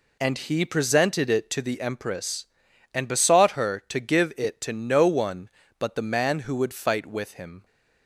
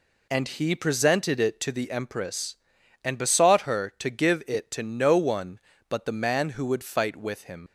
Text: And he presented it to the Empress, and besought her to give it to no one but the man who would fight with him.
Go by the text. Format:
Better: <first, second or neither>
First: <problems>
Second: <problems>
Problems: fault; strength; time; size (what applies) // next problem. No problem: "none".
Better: first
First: none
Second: leaves "him" unfinished; at 7.6 s; 85 ms